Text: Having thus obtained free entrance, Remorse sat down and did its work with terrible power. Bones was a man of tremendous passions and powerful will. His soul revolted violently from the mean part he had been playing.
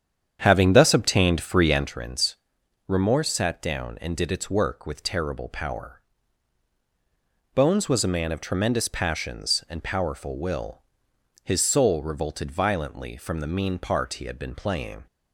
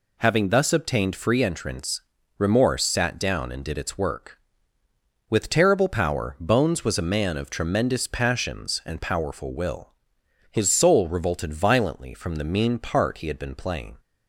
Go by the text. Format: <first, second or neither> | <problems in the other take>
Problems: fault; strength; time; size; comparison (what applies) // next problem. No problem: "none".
second | starts louder than the rest; strong; until 1.9 s; 8.5 dB